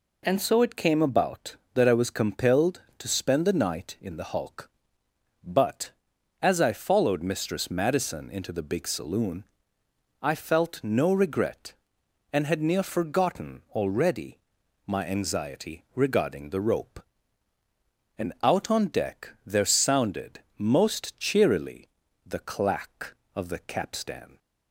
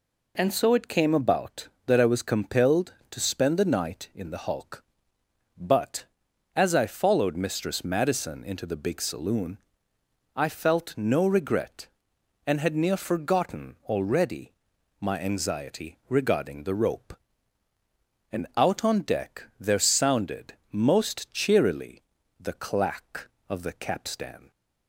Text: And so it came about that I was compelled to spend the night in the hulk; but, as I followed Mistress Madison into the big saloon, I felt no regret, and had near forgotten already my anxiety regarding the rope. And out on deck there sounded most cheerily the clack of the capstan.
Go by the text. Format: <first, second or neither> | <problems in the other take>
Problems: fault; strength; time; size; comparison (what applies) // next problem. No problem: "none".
neither | pauses between "already" and "my"; noticeable; the same in both // pauses between "sounded" and "most"; slight; the same in both // pauses between "cheerily" and "the"; slight; the same in both